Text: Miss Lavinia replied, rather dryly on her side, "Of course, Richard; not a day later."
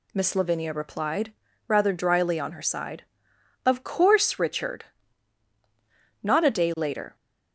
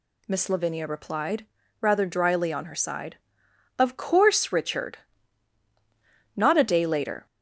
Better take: first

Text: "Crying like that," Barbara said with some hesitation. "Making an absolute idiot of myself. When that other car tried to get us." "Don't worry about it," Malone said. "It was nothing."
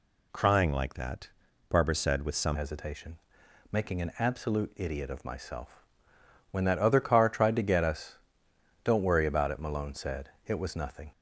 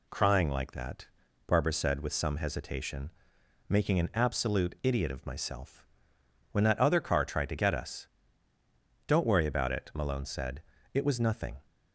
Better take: second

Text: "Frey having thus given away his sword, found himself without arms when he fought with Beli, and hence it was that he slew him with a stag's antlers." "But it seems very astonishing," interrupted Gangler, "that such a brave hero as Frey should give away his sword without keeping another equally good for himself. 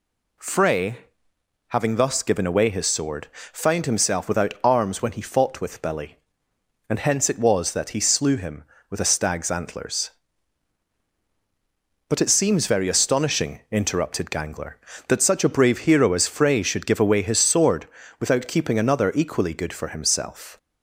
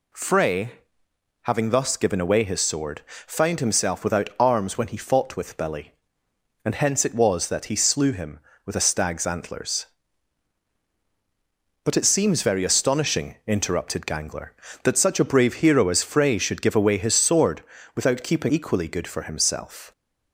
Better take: first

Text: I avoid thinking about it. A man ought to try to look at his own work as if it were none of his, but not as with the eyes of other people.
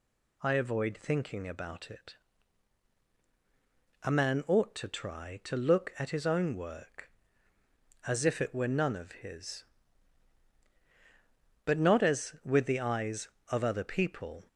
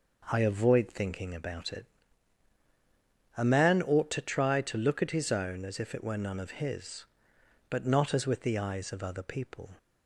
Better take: first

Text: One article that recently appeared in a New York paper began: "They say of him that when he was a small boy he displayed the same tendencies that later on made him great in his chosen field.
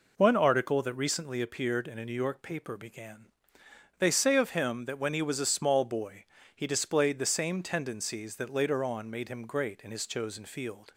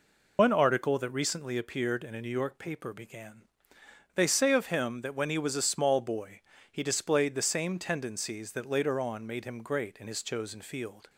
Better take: first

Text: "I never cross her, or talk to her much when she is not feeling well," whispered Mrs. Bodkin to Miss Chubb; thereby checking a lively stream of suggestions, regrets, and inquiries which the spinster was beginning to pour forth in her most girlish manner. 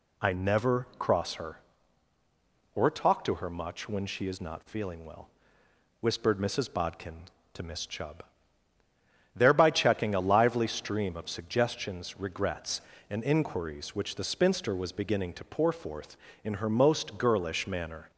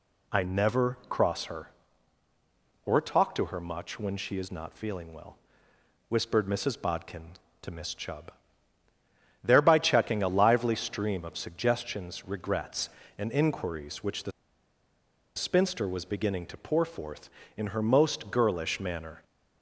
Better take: first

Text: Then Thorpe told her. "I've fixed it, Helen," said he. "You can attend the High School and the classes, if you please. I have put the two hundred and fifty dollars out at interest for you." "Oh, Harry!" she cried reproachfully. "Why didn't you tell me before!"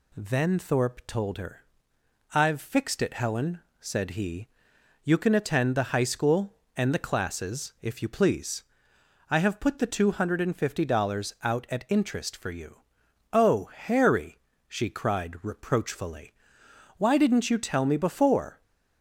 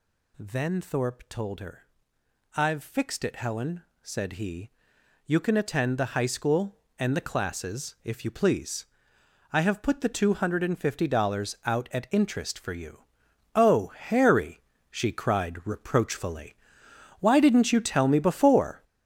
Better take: first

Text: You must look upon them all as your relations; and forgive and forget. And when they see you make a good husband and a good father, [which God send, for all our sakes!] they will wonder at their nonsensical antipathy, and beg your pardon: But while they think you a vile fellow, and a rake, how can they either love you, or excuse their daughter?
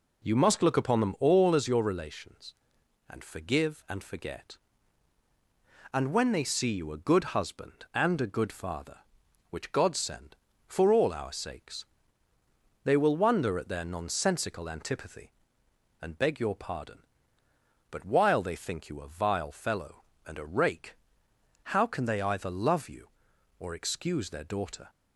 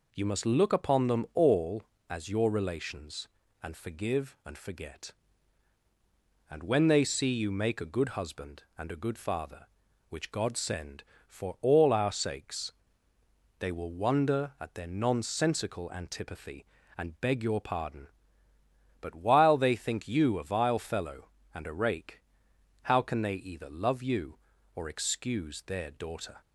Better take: second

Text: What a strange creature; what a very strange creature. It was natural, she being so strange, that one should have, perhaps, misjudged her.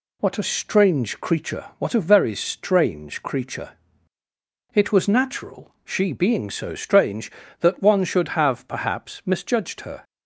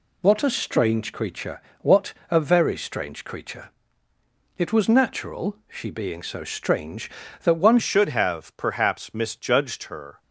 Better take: first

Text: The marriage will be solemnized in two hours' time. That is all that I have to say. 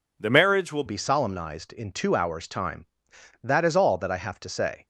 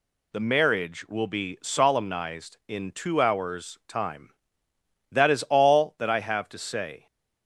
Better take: second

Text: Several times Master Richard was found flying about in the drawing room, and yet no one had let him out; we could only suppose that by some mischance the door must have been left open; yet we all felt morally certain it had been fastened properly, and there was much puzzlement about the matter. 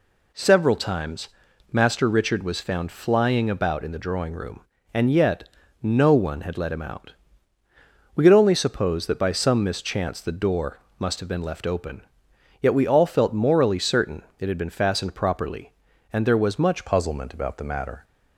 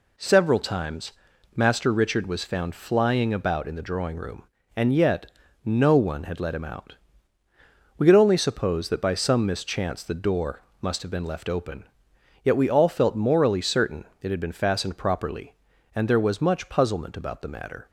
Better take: second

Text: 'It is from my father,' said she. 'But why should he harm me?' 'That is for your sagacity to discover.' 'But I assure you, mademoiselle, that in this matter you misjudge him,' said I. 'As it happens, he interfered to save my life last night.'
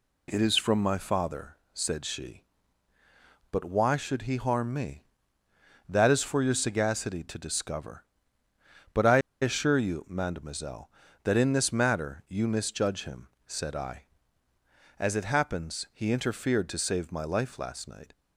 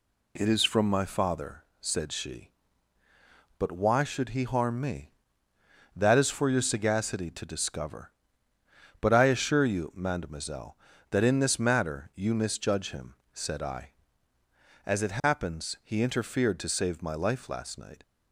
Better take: second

